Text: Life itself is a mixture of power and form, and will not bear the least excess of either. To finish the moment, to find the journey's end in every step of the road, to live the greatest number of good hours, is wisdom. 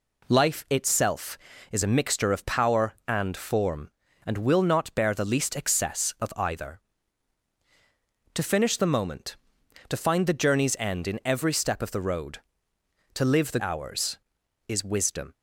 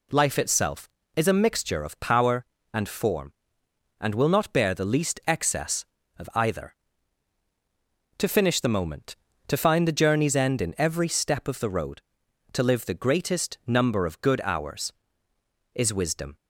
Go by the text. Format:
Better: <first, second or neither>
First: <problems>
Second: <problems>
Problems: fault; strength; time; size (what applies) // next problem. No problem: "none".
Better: second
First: skips "greatest number of good"; at 13.5 s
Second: none